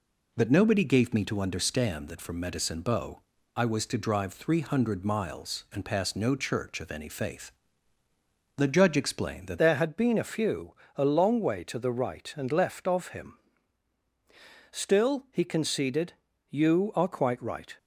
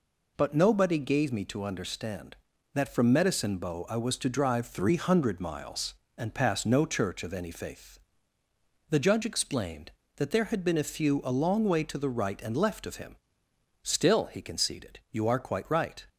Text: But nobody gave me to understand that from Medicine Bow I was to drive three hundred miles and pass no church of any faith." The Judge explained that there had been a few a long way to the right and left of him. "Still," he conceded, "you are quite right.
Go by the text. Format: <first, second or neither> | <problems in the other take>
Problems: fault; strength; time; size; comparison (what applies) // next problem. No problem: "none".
second | pauses between "Bow" and "I"; slight; at 3.2 s; 0.34 s long // changes voice at "there"; from 9.5 s on; 8.2 s long // pauses between "few" and "a"; slight; at 10.7 s; 0.22 s long